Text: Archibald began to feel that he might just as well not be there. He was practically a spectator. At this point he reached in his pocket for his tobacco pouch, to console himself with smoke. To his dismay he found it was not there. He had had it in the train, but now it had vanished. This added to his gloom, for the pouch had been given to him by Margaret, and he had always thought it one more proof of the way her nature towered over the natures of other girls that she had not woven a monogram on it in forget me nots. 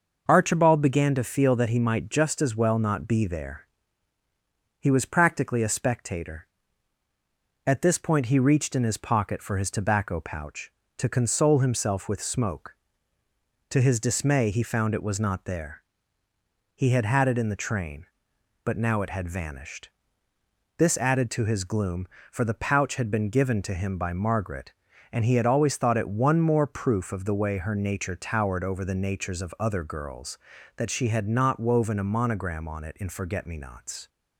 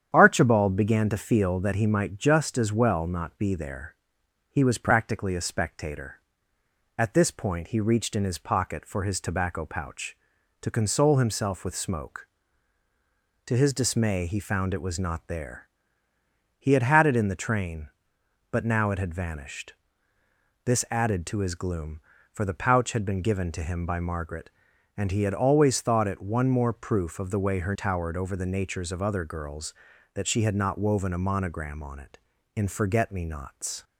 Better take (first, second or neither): first